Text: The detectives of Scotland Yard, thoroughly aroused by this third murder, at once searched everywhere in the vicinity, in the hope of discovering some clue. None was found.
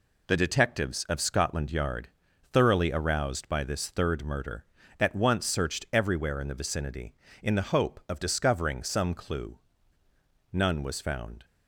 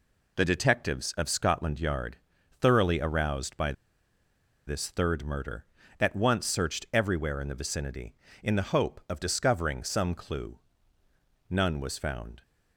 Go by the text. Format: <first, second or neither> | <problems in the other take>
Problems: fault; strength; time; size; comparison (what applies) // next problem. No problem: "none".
first | pauses between "by" and "this"; noticeable; at 3.7 s; 0.95 s long